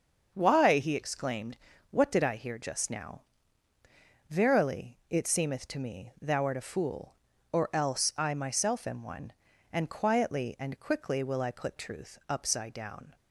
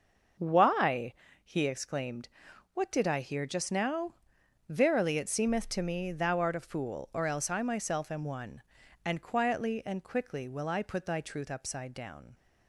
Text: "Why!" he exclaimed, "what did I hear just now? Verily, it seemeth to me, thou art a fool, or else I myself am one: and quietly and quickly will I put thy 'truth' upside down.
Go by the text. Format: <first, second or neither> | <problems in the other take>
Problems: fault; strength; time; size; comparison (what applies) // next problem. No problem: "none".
second | starts louder than the rest; until 1.3 s; 6.5 dB; noticeable in the second // skips "thy"; at 11.7 s